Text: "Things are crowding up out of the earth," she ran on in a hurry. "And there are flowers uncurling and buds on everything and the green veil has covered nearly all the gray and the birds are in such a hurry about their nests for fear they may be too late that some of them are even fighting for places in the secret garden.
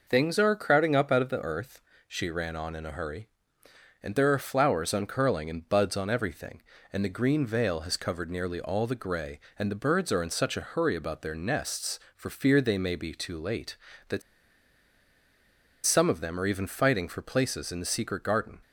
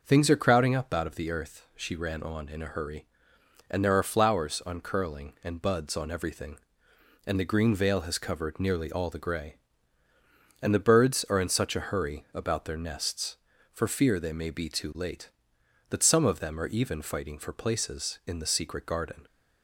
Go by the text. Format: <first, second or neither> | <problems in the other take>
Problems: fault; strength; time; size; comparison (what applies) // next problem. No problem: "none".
second | pauses between "that" and "some"; strong; at 14.2 s; 1.6 s long